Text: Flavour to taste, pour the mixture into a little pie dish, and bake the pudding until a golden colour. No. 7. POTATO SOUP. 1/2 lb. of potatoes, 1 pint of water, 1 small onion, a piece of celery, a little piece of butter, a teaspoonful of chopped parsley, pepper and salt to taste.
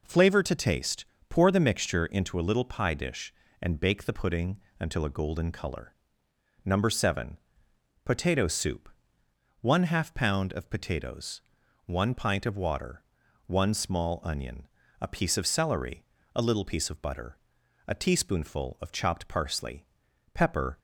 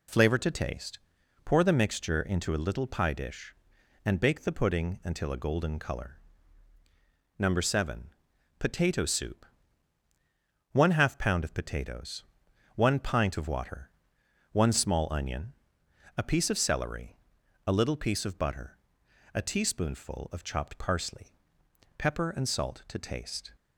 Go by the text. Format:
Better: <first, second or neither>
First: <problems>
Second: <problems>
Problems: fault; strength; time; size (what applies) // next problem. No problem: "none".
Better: second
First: pauses between "pudding" and "until"; slight; at 4.5 s; 0.20 s long // stops before "and salt to taste"; at 20.7 s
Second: none